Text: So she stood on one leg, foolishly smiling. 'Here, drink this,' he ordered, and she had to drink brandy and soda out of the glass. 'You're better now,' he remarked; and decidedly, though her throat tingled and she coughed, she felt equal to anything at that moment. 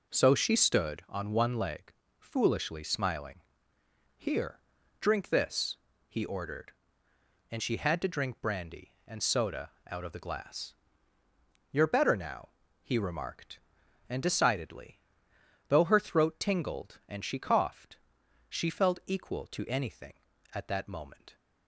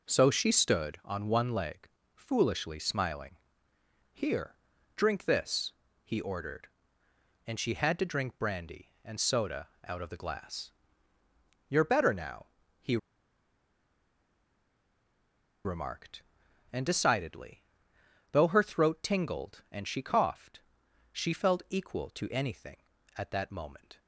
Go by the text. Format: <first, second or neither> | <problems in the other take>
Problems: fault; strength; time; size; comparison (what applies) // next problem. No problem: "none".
first | pauses between "soda" and "out"; slight; at 9.6 s; 0.16 s long; slight in the first // pauses between "he" and "remarked"; strong; at 12.9 s; 2.6 s long